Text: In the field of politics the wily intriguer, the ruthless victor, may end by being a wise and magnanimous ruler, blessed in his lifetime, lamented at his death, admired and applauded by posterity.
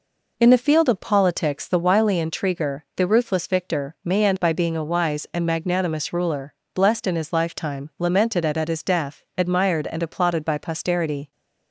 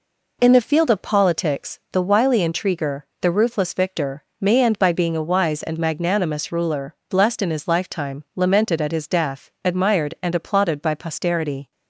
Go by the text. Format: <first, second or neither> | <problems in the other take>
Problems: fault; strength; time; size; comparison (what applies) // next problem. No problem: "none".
second | says "at" twice; at 8.5 s